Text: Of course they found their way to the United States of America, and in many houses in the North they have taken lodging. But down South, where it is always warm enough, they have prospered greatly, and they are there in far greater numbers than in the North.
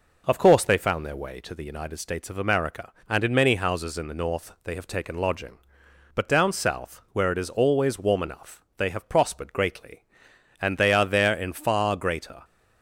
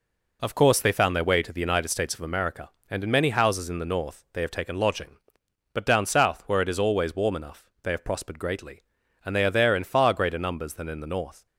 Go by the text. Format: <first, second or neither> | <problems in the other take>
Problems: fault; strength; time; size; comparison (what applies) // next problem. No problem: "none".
second | stops before "numbers than in the North"; at 12.4 s